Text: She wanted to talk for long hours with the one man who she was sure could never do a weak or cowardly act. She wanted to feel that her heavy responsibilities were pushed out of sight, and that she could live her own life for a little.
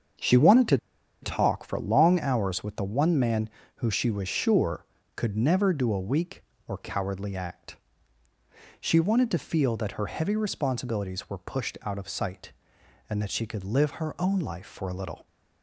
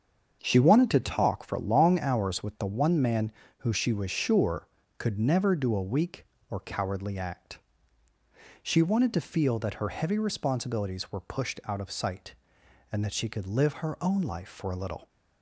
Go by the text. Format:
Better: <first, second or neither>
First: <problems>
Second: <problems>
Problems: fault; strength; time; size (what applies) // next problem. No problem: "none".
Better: second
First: starts louder than the rest; until 1.6 s; 7 dB // pauses between "to" and "talk"; at 0.7 s; 0.44 s long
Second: starts louder than the rest; until 1.4 s; 7 dB